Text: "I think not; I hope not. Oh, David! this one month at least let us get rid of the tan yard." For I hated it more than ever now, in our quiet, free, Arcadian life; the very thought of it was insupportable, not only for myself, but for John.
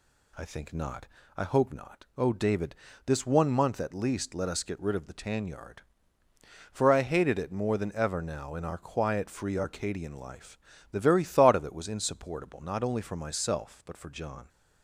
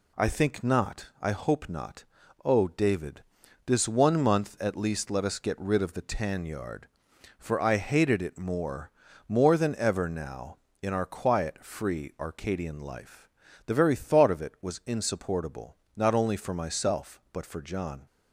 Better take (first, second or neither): first